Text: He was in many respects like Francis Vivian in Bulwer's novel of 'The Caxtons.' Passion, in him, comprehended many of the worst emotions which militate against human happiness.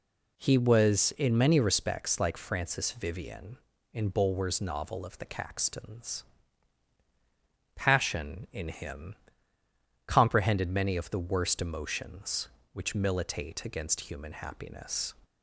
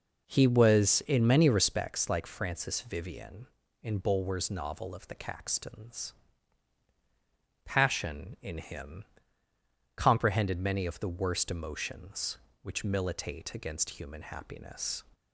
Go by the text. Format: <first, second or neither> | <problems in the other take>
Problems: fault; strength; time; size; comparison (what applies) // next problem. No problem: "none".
first | starts louder than the rest; noticeable; until 2.0 s; 5 dB